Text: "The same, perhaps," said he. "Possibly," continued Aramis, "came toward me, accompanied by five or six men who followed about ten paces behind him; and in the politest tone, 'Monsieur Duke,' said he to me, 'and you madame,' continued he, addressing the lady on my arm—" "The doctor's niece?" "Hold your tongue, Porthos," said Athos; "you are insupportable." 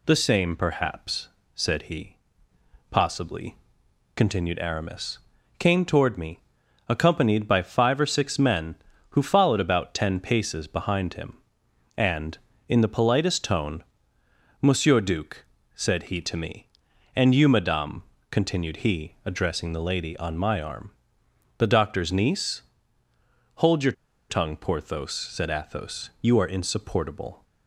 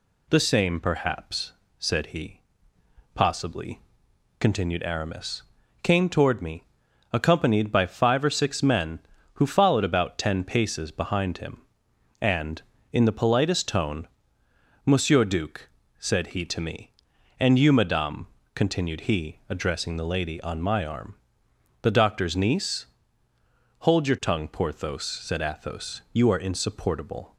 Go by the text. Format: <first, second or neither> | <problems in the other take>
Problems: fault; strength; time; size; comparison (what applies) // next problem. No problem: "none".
second | pauses between "your" and "tongue"; at 23.9 s; 0.38 s long